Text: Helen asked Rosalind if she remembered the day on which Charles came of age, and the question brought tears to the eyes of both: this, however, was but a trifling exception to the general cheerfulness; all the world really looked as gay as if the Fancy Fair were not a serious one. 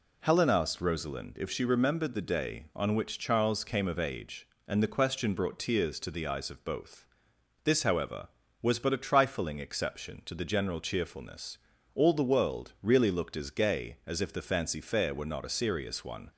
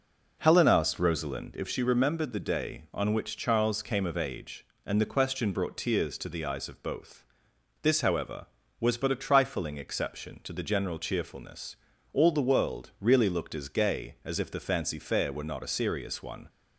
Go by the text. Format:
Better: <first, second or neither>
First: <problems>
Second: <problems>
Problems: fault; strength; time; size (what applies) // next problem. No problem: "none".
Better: first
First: none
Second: starts louder than the rest; noticeable; until 1.6 s; 5 dB